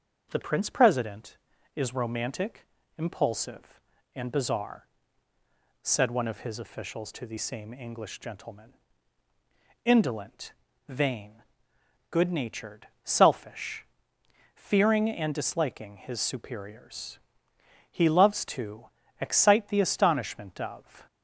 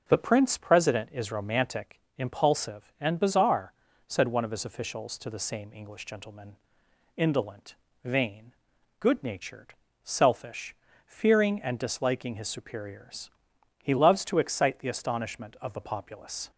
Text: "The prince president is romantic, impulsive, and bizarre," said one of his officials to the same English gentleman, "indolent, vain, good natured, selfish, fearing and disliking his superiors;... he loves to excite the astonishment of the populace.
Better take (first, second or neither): second